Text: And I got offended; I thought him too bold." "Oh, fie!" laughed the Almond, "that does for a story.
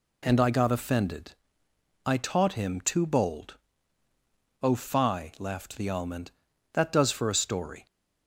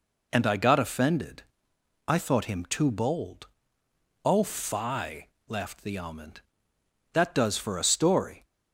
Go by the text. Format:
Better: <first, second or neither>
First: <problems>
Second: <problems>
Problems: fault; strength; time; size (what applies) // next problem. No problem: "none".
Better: second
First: says "taught" for "thought"; at 2.1 s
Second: none